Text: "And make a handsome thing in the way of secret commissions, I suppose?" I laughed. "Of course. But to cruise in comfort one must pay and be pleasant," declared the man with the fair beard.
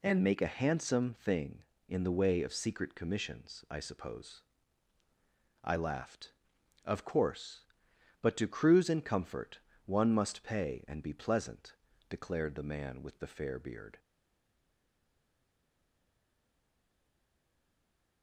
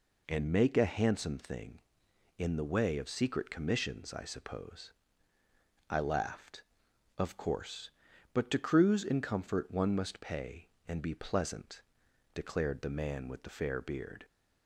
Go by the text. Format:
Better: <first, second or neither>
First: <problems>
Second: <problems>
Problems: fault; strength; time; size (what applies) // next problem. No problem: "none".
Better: second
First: pauses between "comfort" and "one"; slight; at 9.5 s; 0.26 s long // stays silent after the last word; strong; from 13.9 s on; 4.3 s long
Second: none